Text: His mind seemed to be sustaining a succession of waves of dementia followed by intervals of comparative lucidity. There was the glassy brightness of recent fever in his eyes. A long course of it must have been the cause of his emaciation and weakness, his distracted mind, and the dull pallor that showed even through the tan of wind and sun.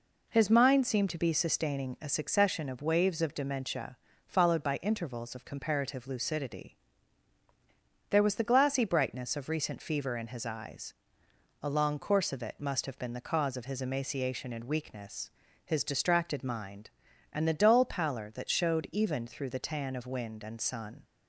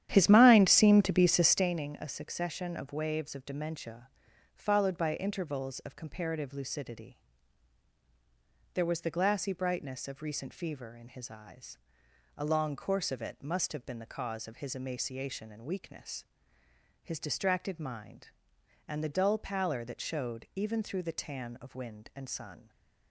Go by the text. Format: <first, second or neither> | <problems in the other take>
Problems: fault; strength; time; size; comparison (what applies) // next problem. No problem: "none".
first | starts louder than the rest; strong; until 1.7 s; 10.5 dB // pauses between "dementia" and "followed"; noticeable; at 4.0 s; 0.48 s long; slight in the first